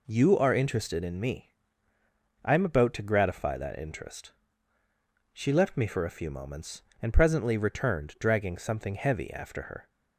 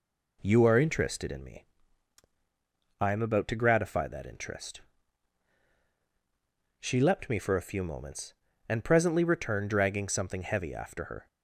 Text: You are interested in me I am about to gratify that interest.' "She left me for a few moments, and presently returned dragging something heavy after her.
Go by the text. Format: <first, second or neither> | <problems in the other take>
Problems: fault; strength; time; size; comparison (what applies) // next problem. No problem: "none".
first | pauses between "me" and "I"; strong; at 1.6 s; 1.3 s long; noticeable in the first // says "leapt" for "left"; at 6.9 s